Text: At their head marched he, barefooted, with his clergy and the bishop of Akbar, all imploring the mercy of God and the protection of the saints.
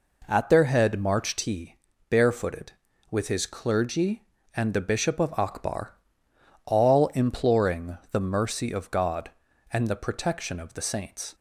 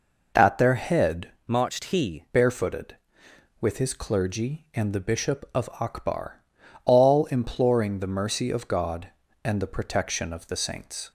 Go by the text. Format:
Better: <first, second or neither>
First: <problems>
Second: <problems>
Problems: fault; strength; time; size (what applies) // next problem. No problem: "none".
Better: first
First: none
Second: changes voice from "marched" to "he"; from 1.4 to 2.2 s; 0.8 s long